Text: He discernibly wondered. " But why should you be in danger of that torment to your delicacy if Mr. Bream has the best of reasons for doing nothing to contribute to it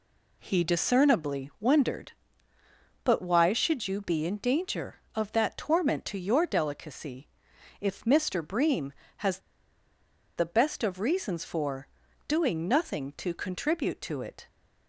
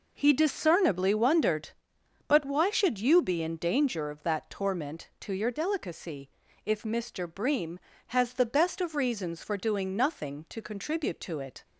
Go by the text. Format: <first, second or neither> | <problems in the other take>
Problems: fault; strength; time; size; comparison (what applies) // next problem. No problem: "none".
second | pauses between "delicacy" and "if"; noticeable; at 7.2 s; 0.54 s long; slight in the second // pauses between "has" and "the"; noticeable; at 9.3 s; 0.97 s long // pauses between "for" and "doing"; at 11.8 s; 0.40 s long